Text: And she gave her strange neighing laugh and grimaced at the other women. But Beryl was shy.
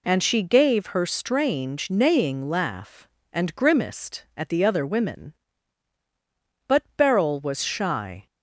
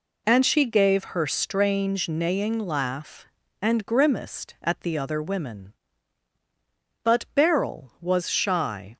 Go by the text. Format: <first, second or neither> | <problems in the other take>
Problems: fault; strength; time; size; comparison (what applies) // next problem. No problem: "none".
neither | none